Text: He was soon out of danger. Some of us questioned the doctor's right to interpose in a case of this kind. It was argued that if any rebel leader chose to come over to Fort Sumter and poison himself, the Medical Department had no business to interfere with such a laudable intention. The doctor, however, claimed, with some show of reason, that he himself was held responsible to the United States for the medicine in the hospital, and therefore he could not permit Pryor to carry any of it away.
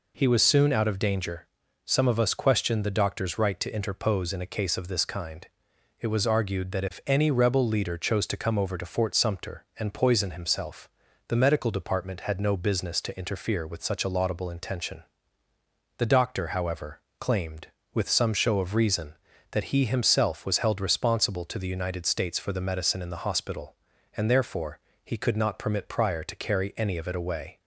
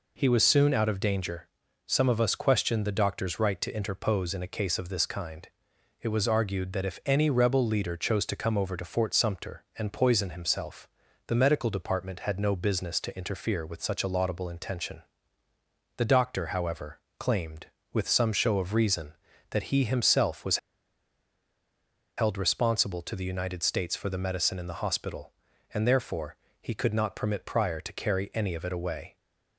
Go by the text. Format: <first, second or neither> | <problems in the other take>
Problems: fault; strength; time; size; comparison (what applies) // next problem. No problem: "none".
first | pauses between "was" and "held"; strong; at 20.5 s; 1.6 s long // pauses between "therefore" and "he"; slight; at 26.3 s; 0.24 s long; slight in the first